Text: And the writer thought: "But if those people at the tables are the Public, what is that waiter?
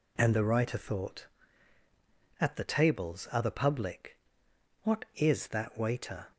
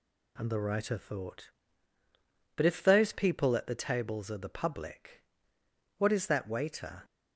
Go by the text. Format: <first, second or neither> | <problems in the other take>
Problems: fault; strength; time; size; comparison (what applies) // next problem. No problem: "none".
second | skips "But if those people"; at 1.8 s